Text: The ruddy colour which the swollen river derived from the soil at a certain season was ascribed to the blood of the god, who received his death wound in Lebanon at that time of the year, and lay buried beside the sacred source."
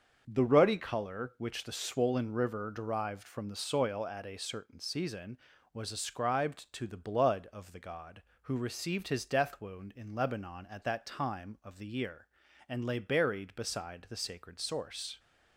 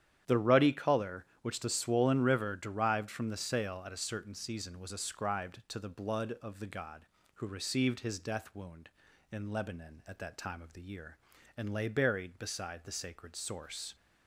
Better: first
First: starts louder than the rest; until 1.2 s; 6.5 dB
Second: starts louder than the rest; strong; until 1.4 s; 10 dB // says "sail" for "soil"; at 3.3 s

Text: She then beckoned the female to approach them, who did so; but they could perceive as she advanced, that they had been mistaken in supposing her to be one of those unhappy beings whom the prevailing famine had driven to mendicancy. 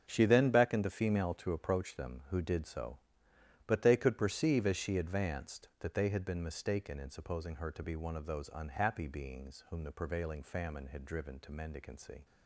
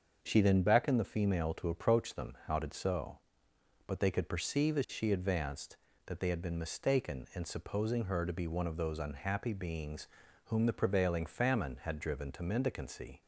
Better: first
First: starts louder than the rest; until 1.0 s; 7 dB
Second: starts louder than the rest; until 1.2 s; 6.5 dB // says "how" for "who"; at 2.4 s // pauses between "beings" and "whom"; at 10.0 s; 0.38 s long

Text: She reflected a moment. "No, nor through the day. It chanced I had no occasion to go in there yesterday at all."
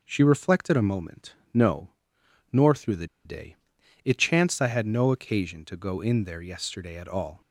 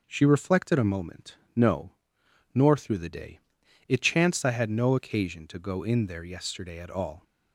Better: second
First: pauses between "the" and "day"; slight; at 3.0 s; 0.19 s long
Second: none

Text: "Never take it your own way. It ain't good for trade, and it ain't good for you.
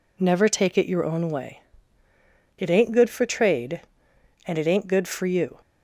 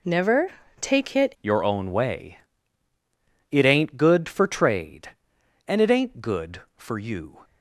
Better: first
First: none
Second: pauses between "Never" and "take"; slight; at 0.5 s; 0.30 s long // changes voice at "your"; from 1.4 s on; 6.0 s long

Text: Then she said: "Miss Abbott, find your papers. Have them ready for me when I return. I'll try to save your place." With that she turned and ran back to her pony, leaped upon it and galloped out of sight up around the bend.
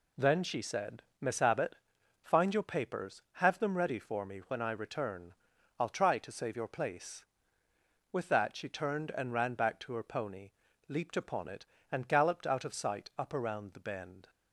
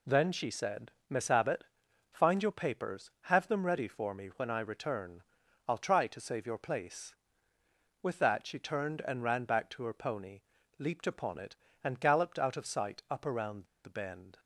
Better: first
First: none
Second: pauses between "around" and "the"; slight; at 13.6 s; 0.18 s long

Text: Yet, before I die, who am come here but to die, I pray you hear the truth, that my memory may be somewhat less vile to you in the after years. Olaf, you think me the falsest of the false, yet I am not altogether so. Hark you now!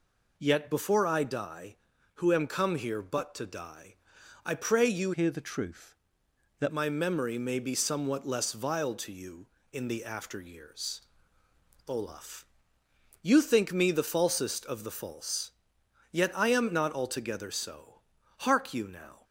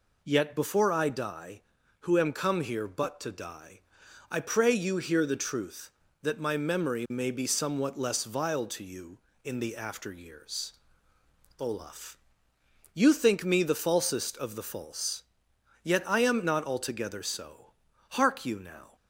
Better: second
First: changes voice from "hear" to "that"; from 5.1 to 6.7 s; 1.6 s long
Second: none

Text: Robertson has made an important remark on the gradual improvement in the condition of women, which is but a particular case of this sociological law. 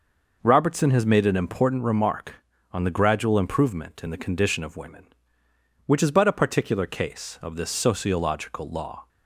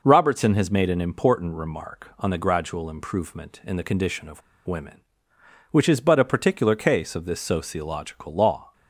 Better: first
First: none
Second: pauses between "of" and "women"; slight; at 4.4 s; 0.27 s long

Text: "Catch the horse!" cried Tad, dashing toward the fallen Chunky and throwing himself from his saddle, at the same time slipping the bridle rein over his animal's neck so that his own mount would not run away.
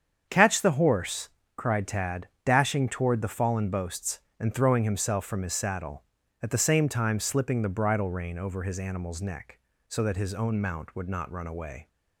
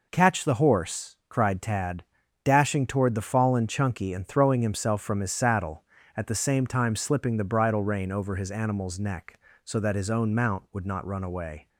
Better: second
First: starts louder than the rest; strong; until 1.3 s; 7.5 dB // says "Boasts" for "Chunky"; at 3.6 s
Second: none

